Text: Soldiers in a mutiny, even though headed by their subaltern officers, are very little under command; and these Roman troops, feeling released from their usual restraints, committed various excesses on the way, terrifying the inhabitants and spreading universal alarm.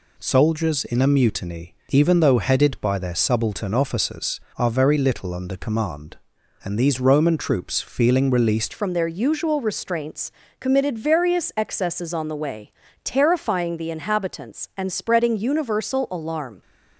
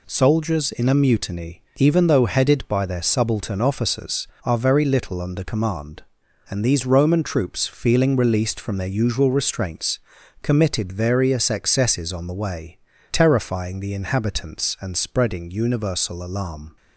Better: second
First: changes voice at "from"; from 8.7 s on; 7.9 s long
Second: none

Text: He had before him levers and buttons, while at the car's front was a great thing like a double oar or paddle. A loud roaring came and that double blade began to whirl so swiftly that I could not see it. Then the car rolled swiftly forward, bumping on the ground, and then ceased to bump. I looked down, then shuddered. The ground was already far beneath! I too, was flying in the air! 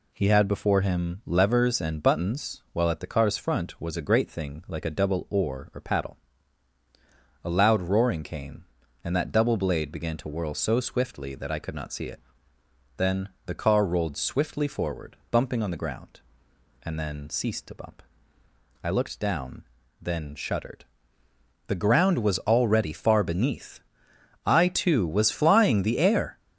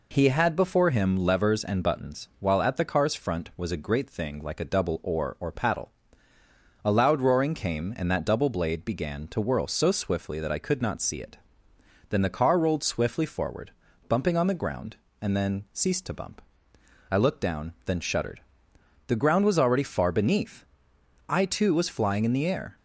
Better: second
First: pauses between "Then" and "the"; slight; at 13.2 s; 0.18 s long // skips "in"; at 25.8 s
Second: none

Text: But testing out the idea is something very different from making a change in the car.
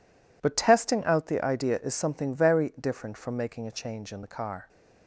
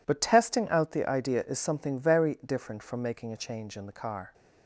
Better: neither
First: none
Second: none

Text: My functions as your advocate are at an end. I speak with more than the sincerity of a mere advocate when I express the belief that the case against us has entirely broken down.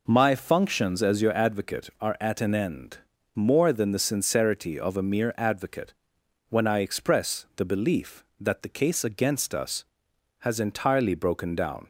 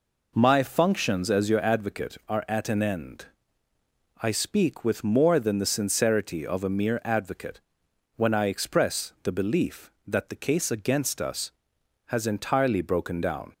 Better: second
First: skips "I speak with"; at 3.1 s // pauses between "advocate" and "when"; noticeable; at 5.9 s; 0.54 s long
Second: pauses between "advocate" and "when"; noticeable; at 7.6 s; 0.54 s long

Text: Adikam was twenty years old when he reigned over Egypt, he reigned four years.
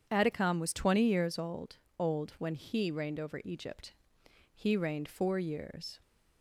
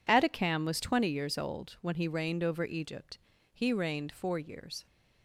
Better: second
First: says "old" twice; at 1.9 s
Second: none

